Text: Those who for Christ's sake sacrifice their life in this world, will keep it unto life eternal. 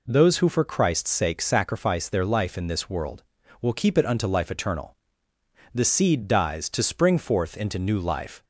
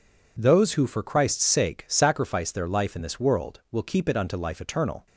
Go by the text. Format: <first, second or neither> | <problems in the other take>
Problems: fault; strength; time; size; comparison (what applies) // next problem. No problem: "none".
second | goes on to say "The seed dies to spring forth into new life"; strong; from 5.7 s on; 2.7 s long